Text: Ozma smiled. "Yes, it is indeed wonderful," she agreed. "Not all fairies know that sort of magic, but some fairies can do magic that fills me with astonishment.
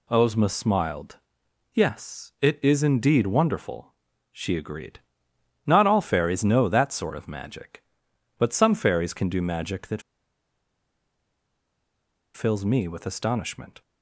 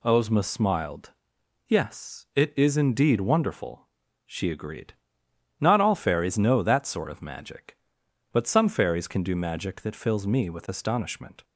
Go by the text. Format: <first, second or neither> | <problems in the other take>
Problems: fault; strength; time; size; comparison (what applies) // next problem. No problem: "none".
second | pauses between "that" and "fills"; strong; at 10.0 s; 2.3 s long